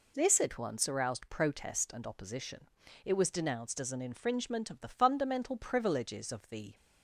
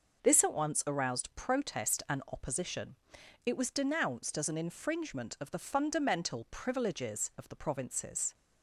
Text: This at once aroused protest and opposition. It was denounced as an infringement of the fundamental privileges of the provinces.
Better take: second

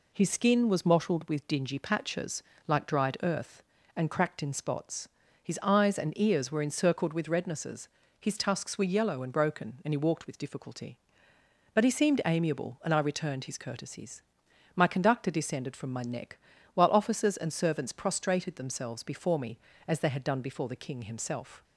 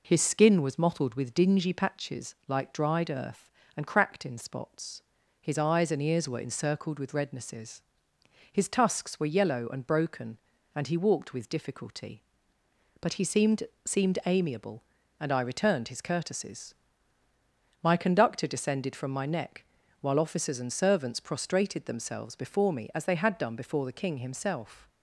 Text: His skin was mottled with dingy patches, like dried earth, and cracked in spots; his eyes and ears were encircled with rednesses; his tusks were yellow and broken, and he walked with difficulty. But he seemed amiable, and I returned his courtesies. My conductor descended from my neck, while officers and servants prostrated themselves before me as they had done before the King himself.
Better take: first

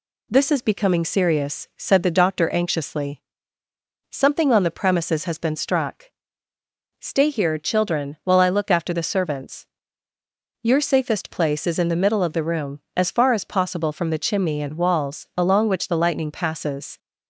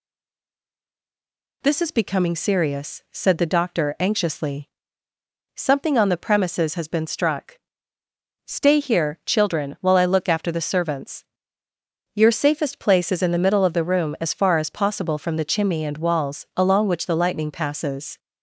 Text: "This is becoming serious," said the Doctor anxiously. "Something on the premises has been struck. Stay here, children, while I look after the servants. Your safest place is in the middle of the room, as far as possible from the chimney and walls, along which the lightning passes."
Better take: first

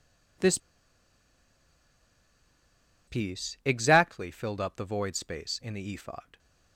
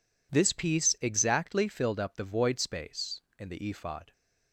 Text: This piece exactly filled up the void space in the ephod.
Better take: second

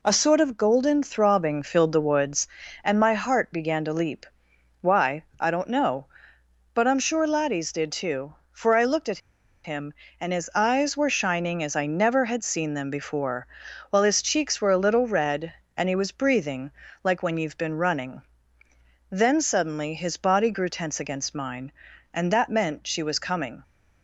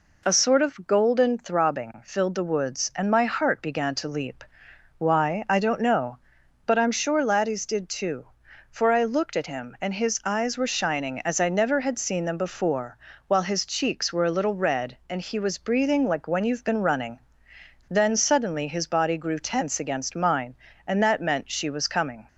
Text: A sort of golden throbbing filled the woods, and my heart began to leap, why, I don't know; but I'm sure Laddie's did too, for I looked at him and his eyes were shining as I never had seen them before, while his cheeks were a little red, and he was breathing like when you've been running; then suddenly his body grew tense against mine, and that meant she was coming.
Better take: second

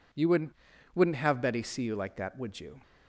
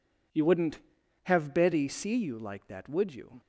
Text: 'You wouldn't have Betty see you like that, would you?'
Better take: second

